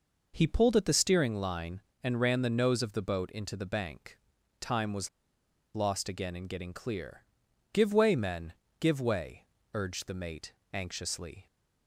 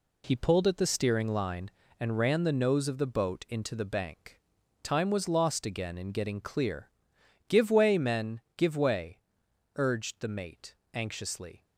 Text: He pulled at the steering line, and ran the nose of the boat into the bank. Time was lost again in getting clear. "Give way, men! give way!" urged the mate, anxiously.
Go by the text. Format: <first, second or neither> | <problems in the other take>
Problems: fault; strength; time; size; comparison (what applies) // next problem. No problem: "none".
second | pauses between "was" and "lost"; noticeable; at 5.0 s; 0.65 s long